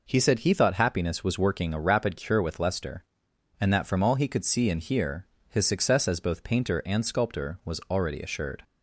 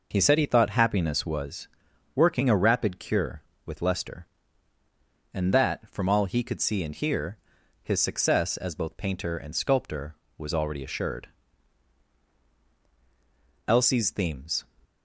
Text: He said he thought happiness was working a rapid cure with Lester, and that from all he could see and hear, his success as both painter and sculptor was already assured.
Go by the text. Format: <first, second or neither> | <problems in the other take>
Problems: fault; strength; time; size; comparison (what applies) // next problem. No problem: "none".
first | pauses between "was" and "working"; noticeable; at 1.6 s; 0.48 s long // goes on to say "Elsie's themes"; noticeable; from 13.6 s on; 1.0 s long